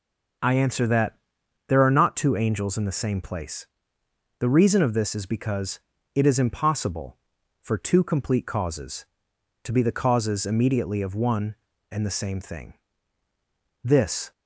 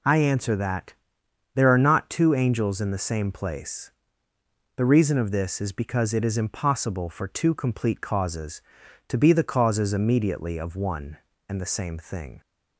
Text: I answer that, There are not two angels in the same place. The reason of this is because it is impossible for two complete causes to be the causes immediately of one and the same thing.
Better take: second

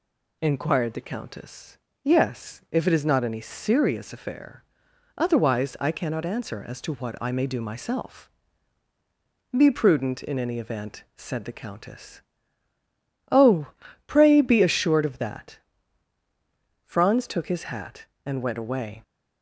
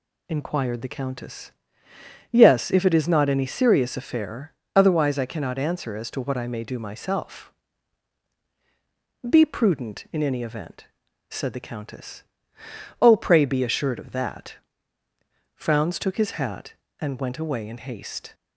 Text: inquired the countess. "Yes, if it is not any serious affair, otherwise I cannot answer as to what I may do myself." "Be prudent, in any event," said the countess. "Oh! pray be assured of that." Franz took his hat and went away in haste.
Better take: second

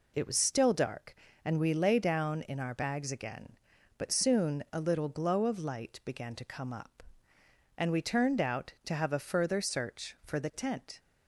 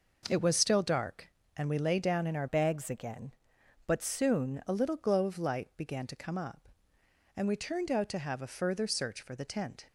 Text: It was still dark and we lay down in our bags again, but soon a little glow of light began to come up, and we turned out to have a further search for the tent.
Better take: first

